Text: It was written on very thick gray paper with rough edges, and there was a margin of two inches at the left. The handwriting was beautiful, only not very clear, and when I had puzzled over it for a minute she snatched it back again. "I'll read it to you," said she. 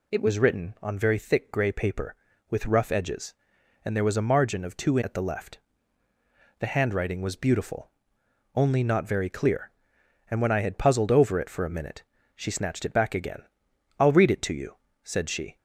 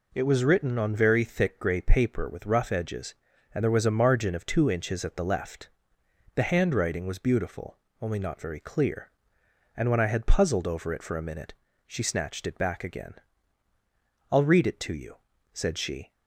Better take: second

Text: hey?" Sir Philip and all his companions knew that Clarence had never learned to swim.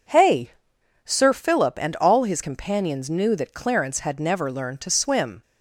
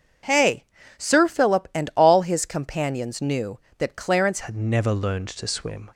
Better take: first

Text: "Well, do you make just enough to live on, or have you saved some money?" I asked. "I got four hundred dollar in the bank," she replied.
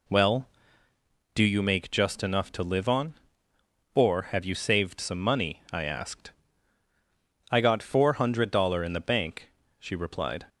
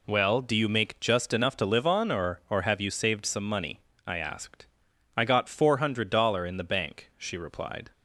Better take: first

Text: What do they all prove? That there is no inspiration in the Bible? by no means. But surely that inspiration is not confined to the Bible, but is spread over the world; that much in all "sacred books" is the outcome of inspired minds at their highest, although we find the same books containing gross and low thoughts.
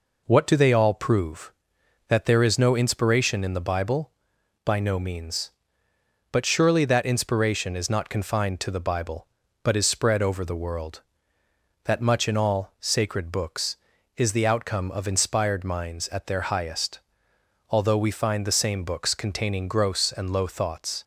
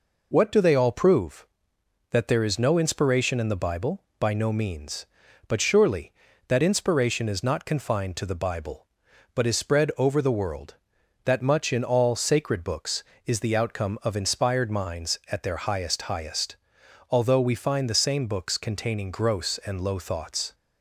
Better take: first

